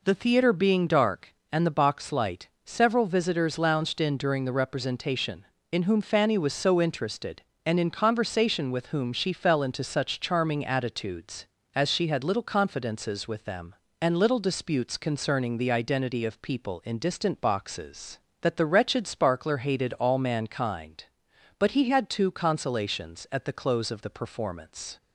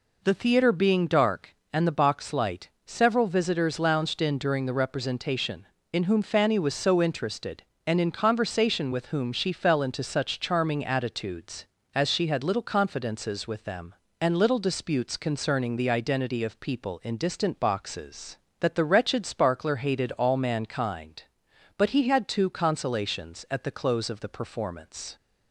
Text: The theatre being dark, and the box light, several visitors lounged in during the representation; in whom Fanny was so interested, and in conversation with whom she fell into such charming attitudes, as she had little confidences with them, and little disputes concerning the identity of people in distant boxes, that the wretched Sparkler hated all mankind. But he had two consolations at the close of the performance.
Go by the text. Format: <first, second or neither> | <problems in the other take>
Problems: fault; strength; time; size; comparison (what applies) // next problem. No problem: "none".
neither | none